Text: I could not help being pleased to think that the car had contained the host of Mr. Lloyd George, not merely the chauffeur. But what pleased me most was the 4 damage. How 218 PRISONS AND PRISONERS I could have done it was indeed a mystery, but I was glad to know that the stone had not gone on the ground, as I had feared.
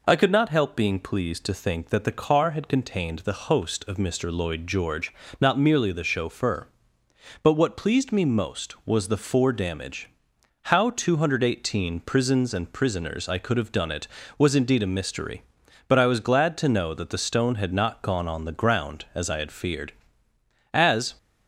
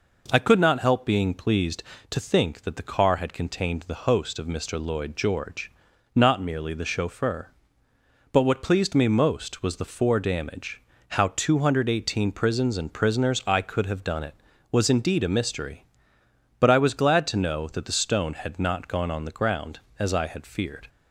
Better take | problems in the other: second | goes on to say "As"; slight; from 20.7 s on; 0.42 s long

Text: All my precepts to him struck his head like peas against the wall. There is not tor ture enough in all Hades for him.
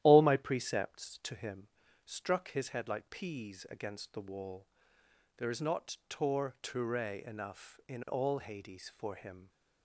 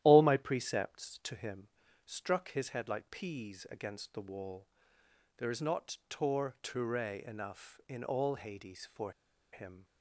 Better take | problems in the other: first | starts louder than the rest; strong; until 1.0 s; 12 dB; strong in the first // pauses between "him" and "struck"; at 1.6 s; 0.40 s long; also in the first // pauses between "for" and "him"; at 9.1 s; 0.41 s long

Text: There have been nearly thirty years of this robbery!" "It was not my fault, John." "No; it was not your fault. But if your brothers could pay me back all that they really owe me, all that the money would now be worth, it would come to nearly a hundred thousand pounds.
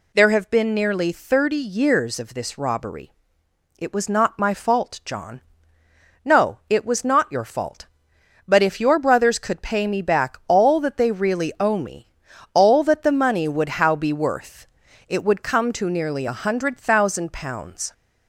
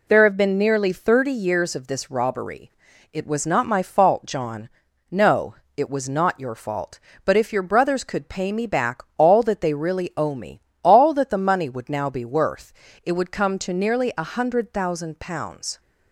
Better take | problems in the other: second | says "how" for "now"; at 13.7 s

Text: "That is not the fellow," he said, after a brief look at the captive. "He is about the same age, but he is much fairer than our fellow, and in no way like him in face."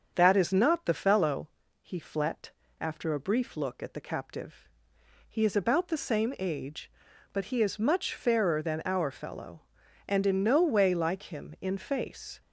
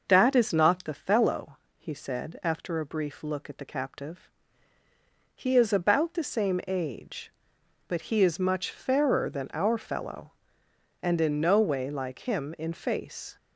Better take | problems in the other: second | starts louder than the rest; until 1.1 s; 7 dB // says "flet" for "said"; at 1.9 s

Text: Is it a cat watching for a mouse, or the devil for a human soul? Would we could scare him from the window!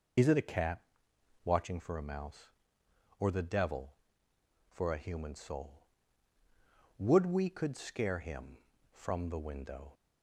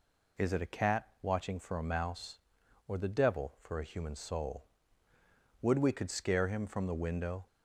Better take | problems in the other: second | loses the start of "Is"; at 0.1 s; 40 ms // pauses between "cat" and "watching"; noticeable; at 0.8 s; 0.64 s long; slight in the second

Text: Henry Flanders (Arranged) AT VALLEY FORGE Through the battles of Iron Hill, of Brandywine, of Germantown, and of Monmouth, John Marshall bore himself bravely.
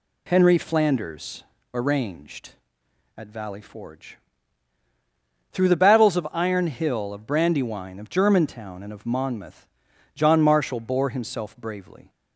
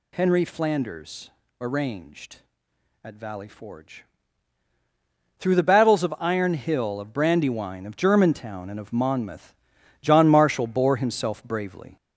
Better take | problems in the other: first | gets louder; noticeable; throughout; 4.5 dB // pauses between "FORGE" and "Through"; strong; at 4.0 s; 1.3 s long; strong in the first

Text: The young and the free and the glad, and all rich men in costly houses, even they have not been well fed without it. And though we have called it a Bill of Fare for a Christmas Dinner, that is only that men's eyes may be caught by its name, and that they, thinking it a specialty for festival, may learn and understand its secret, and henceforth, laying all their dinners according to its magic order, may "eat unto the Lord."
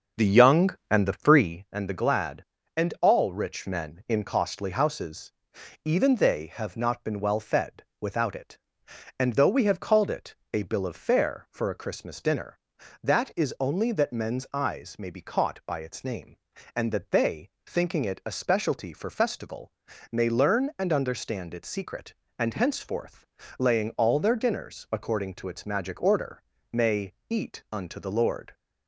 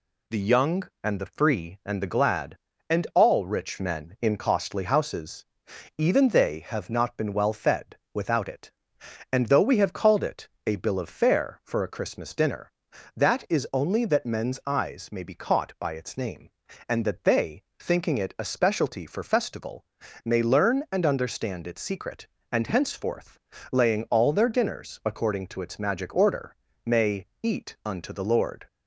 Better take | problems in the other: second | starts louder than the rest; until 1.7 s; 7 dB // pauses between "fed" and "without"; slight; at 7.8 s; 0.16 s long; slight in the second // pauses between "it" and "a"; slight; at 10.3 s; 0.16 s long; slight in the second // pauses between "may" and "eat"; slight; at 27.1 s; 0.18 s long; slight in the second

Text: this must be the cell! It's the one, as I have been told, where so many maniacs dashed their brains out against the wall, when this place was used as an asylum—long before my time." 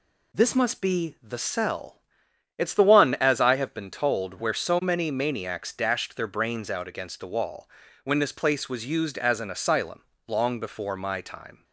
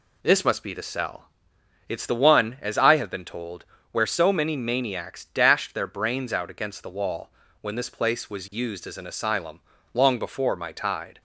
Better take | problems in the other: first | says "tide" for "time"; at 10.7 s

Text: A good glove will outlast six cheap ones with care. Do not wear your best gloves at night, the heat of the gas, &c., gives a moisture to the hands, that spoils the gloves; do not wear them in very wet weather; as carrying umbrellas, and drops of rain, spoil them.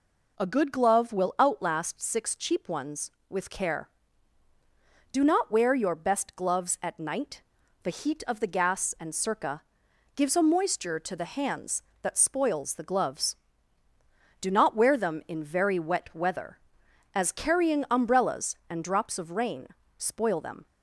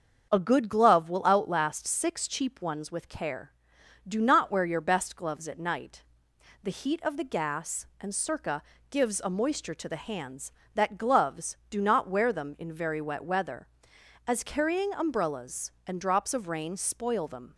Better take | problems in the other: first | starts louder than the rest; until 1.3 s; 7 dB // skips "spoils the"; at 10.9 s

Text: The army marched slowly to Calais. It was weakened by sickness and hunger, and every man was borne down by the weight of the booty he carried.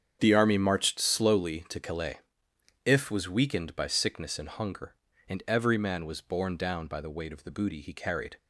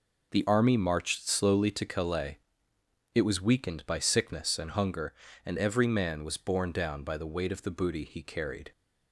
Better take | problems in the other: second | starts louder than the rest; strong; until 1.2 s; 8 dB // says "If" for "It"; at 2.8 s

